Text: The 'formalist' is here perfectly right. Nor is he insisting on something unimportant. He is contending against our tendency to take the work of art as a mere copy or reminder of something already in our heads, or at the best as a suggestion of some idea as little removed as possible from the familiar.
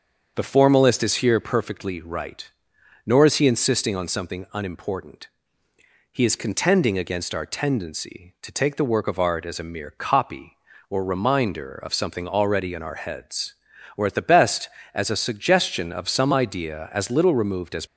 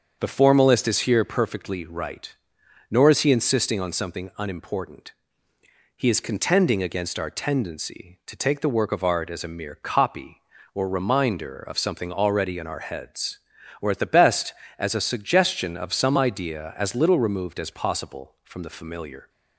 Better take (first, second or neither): second